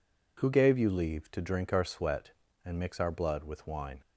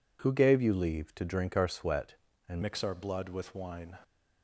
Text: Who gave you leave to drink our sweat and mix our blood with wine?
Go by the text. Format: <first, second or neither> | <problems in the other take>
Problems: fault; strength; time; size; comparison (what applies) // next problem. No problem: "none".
first | changes voice at "mix"; from 2.6 s on; 1.3 s long